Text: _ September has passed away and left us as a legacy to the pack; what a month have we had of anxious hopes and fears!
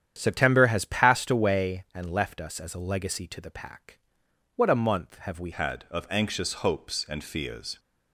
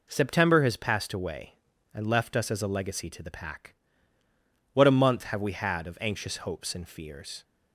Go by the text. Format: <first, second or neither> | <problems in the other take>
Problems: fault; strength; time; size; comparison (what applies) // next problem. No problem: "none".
second | starts louder than the rest; strong; until 1.1 s; 9.5 dB // changes voice at "had"; from 5.5 s on; 2.2 s long